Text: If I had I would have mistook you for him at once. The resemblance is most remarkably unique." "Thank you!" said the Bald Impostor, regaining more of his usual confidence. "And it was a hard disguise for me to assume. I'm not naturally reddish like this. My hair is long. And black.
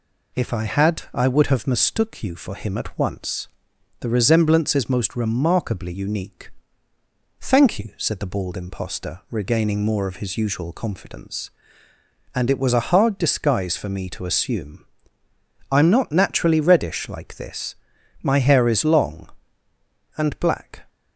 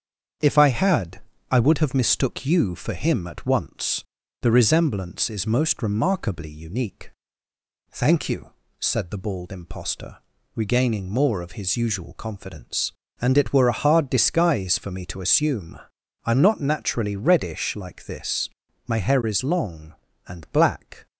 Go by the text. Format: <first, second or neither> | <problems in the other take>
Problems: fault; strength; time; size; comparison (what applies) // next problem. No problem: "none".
first | starts louder than the rest; strong; until 1.7 s; 7.5 dB // pauses between "had" and "I"; slight; at 1.2 s; 0.30 s long // says "were" for "was"; at 13.5 s